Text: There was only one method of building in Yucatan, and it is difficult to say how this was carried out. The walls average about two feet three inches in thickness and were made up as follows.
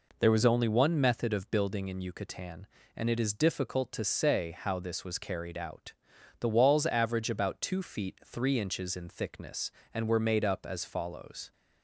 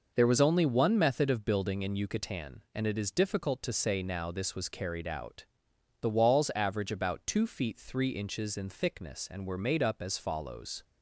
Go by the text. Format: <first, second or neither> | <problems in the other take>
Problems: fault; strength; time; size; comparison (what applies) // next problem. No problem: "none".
first | says "now" for "how"; at 4.0 s